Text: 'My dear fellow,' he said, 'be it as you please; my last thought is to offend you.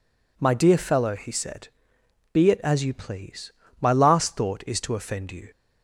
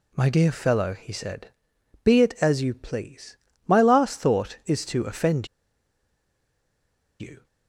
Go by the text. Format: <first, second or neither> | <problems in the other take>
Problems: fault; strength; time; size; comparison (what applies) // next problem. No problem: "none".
first | pauses between "offend" and "you"; strong; at 5.4 s; 1.7 s long